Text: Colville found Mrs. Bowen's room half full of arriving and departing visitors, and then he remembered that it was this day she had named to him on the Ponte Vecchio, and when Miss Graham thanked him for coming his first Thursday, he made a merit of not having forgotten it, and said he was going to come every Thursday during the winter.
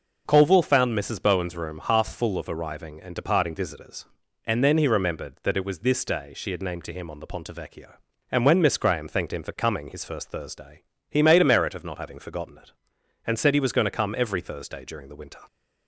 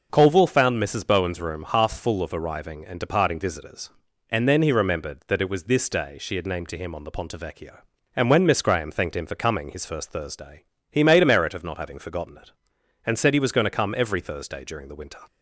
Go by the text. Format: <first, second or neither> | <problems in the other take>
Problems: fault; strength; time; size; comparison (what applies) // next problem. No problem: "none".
neither | none